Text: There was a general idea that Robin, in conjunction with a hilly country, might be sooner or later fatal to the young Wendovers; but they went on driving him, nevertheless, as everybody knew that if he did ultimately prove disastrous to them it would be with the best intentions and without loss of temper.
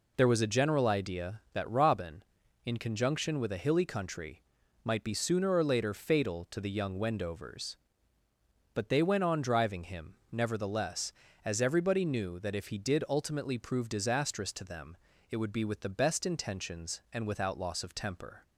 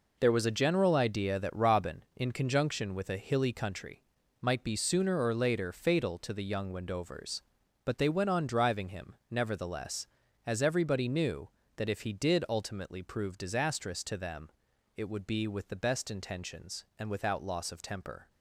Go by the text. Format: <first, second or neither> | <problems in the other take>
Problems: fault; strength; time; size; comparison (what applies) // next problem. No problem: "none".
first | gets quieter; strong; throughout; 9 dB // pauses between "them" and "it"; noticeable; at 14.4 s; 0.48 s long; slight in the first